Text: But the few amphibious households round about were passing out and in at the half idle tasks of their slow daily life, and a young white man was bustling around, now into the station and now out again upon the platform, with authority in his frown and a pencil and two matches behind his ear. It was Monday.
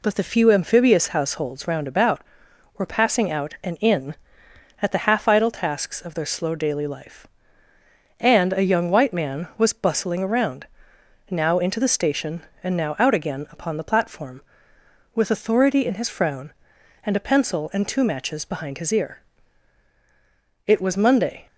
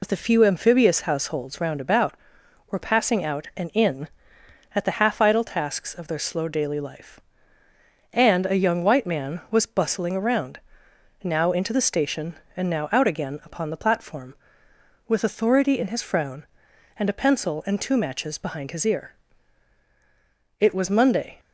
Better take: first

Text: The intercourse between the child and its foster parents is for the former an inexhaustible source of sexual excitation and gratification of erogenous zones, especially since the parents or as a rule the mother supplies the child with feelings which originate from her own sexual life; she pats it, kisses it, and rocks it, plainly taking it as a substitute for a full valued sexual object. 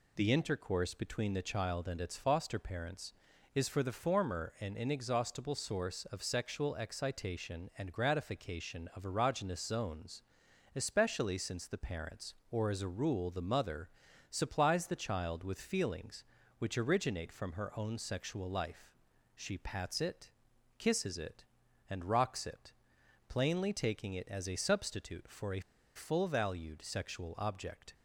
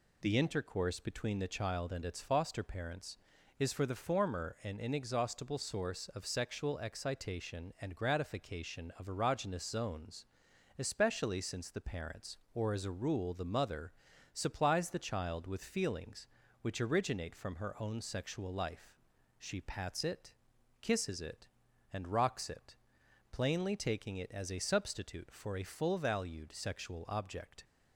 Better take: second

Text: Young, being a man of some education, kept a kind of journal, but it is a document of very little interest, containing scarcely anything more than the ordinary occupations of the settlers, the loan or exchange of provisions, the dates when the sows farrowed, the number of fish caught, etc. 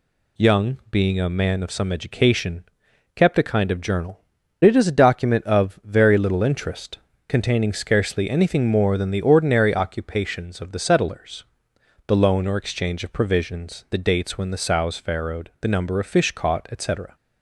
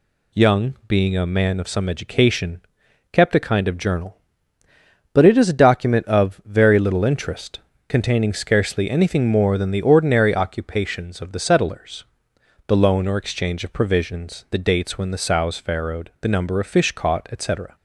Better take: second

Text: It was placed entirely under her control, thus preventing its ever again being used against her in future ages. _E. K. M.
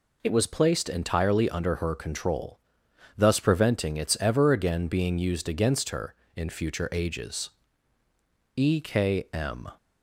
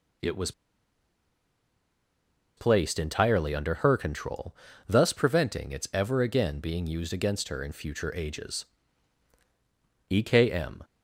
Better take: first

